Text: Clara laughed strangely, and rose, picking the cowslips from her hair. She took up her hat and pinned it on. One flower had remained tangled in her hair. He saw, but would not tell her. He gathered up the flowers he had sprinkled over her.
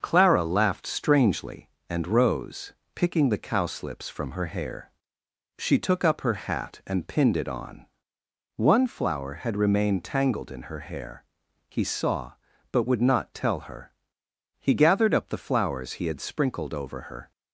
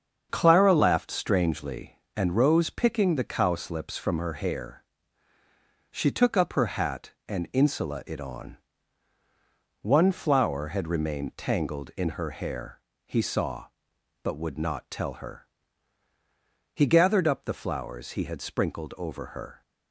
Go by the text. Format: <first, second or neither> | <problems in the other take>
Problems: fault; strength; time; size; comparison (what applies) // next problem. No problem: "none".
first | starts louder than the rest; strong; until 1.3 s; 7 dB; also in the first // says "insula" for "pinned"; at 7.5 s